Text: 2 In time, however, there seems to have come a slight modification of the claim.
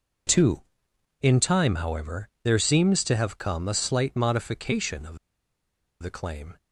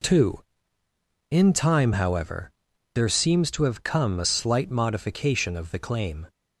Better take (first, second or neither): second